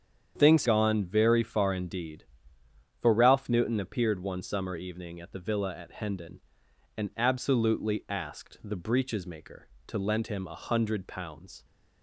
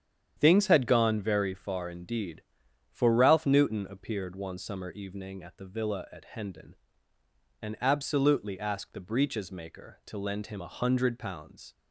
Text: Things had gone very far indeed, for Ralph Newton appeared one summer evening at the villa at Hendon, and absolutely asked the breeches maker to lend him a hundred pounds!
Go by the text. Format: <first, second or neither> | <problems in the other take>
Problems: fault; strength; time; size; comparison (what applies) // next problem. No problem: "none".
second | starts louder than the rest; strong; until 1.3 s; 8.5 dB; strong in the second // skips "had"; at 0.6 s